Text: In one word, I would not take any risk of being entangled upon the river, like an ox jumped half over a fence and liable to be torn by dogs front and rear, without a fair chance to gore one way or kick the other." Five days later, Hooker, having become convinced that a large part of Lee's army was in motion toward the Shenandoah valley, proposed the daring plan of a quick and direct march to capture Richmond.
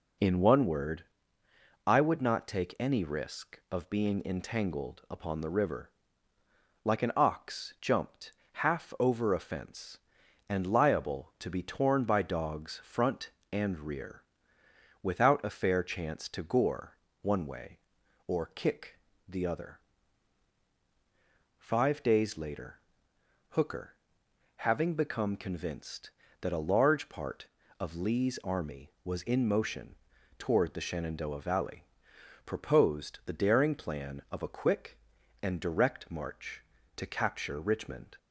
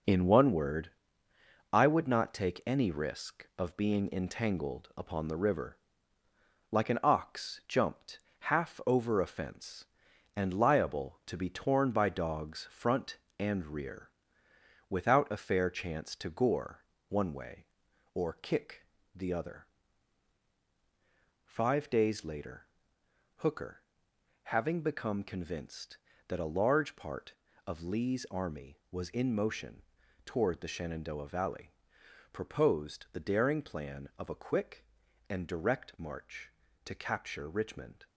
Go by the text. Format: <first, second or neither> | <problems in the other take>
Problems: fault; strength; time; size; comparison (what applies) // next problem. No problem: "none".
first | gets quieter; throughout; 7 dB // pauses between "jumped" and "half"; slight; at 8.1 s; 0.22 s long; slight in the first // pauses between "gore" and "one"; slight; at 16.8 s; 0.26 s long; slight in the first // pauses between "kick" and "the"; slight; at 18.8 s; 0.30 s long; slight in the first // pauses between "motion" and "toward"; at 29.8 s; 0.42 s long; also in the first